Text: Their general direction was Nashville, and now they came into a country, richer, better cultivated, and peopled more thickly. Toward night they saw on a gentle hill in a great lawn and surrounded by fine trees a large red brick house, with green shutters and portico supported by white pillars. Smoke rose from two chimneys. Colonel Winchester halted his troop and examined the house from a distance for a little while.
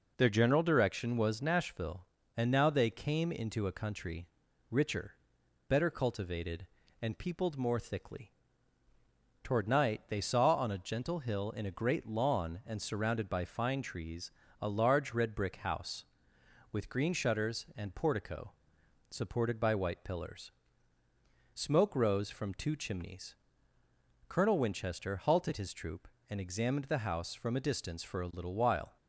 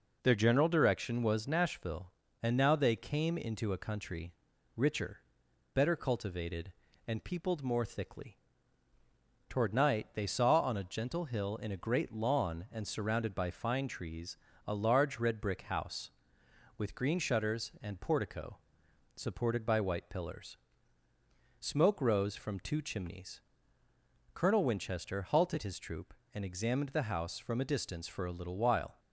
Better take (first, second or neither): neither